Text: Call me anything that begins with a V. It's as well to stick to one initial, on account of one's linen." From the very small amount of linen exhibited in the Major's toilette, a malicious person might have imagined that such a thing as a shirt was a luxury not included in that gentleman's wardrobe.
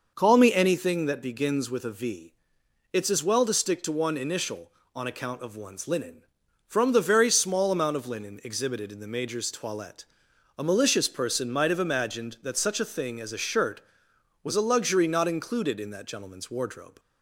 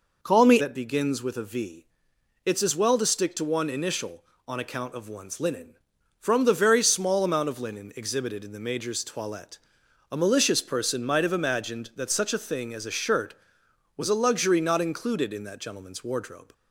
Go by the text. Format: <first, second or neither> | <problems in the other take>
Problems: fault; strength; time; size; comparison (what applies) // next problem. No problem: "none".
first | skips "anything"; at 0.6 s